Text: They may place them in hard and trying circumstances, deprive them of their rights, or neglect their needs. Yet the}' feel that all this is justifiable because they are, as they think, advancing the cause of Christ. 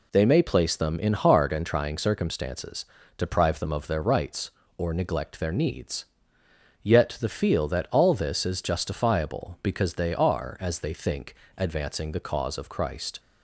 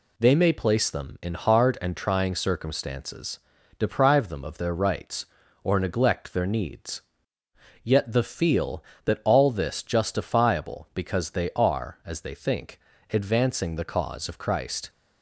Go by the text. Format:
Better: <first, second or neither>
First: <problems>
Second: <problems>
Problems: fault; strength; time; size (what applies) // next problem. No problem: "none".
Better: first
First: none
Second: skips "is"; at 9.8 s